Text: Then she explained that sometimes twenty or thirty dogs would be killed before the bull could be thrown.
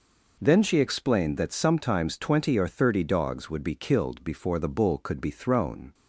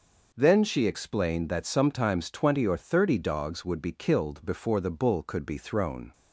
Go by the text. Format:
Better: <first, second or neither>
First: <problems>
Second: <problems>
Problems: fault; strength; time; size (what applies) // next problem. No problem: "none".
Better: neither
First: none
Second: none